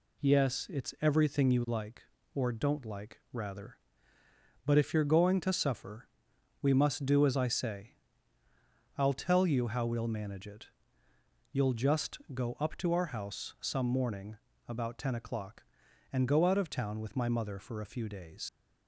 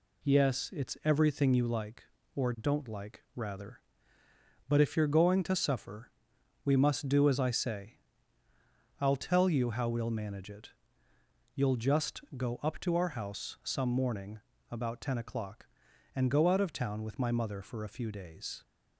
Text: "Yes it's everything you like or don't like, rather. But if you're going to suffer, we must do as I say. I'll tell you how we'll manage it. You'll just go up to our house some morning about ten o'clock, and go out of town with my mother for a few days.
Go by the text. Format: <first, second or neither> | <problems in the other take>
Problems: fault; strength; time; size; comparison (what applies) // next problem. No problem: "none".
second | pauses between "just" and "go"; slight; at 12.1 s; 0.16 s long; slight in the second // pauses between "morning" and "about"; slight; at 14.3 s; 0.32 s long; slight in the second // leaves "days" unfinished; at 18.4 s; 110 ms